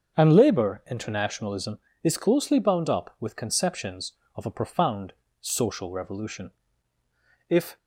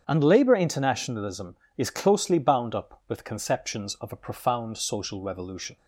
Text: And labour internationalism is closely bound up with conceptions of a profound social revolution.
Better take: second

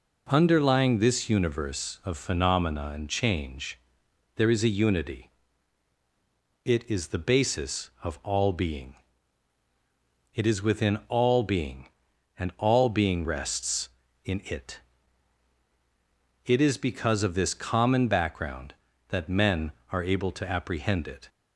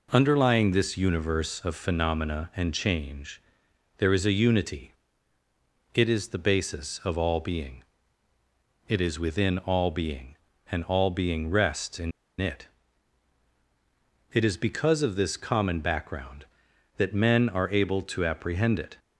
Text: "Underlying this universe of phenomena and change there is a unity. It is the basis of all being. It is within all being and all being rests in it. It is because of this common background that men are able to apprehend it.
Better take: first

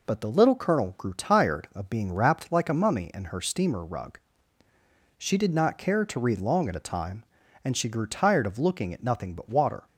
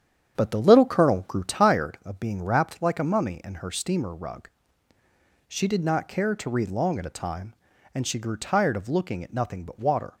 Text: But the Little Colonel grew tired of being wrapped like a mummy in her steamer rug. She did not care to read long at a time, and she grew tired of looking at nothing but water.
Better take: first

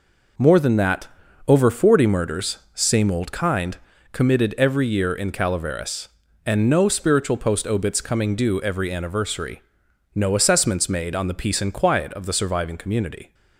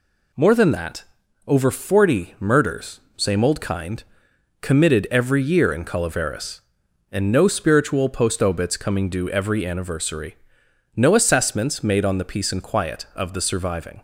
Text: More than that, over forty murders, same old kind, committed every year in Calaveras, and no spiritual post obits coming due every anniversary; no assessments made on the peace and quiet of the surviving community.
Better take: first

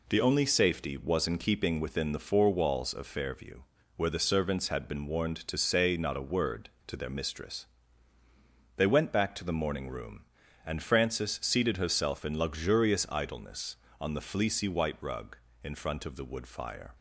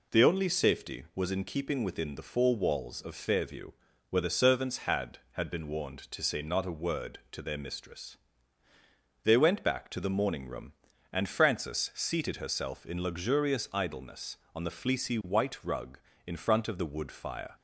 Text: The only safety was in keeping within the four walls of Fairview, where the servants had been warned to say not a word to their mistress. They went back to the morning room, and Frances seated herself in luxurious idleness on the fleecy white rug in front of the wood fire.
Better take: first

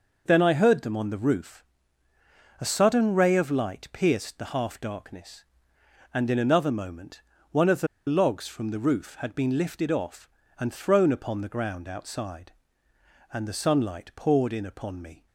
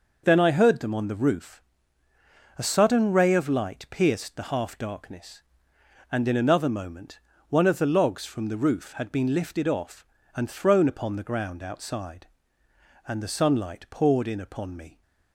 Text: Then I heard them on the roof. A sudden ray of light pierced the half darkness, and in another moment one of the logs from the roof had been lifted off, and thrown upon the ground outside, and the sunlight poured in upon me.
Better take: second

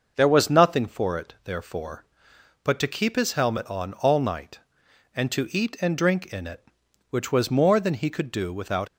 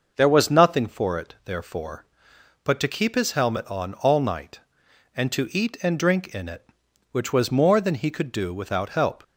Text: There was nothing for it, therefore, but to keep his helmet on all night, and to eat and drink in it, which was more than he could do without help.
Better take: second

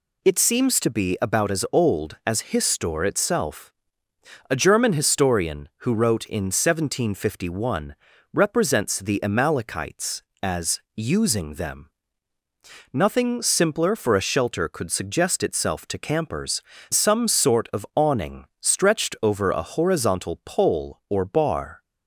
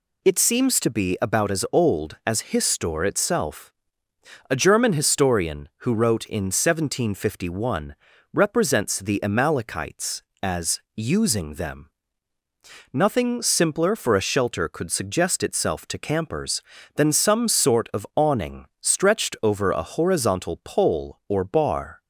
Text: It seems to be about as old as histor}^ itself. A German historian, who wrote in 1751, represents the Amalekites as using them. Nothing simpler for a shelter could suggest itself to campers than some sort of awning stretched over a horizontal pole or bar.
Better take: second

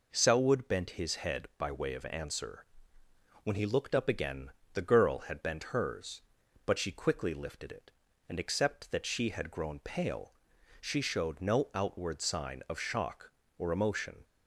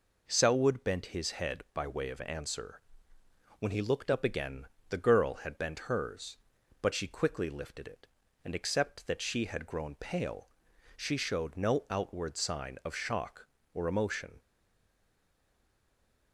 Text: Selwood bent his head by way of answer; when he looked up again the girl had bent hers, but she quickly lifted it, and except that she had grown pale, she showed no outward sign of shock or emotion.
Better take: first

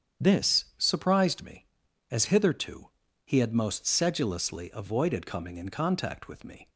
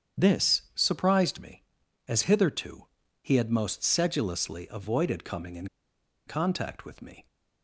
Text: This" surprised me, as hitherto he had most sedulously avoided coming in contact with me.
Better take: first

